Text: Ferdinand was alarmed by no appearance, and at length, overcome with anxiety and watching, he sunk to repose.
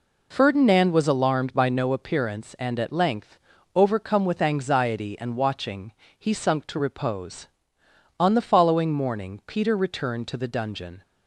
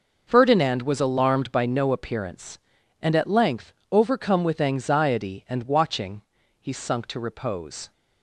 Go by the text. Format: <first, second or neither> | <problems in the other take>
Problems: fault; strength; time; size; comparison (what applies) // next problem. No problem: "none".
second | goes on to say "On the following morning Peter returned to the dungeon"; strong; from 8.1 s on; 2.8 s long